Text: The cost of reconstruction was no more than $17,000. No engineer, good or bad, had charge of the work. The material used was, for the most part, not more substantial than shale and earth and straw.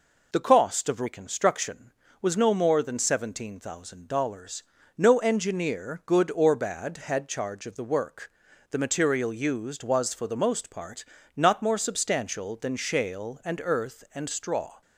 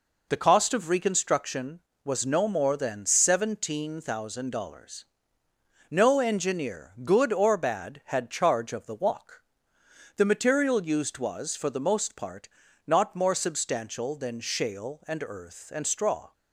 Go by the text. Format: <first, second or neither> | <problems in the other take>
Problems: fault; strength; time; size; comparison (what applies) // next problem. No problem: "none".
first | says "walk" for "work"; at 8.9 s